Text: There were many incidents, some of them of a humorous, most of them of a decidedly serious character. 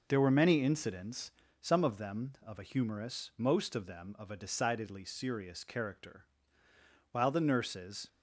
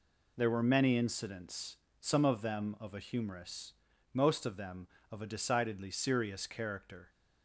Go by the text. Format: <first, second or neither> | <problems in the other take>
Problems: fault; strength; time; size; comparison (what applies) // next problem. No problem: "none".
second | goes on to say "While the nurses"; noticeable; from 7.1 s on; 0.96 s long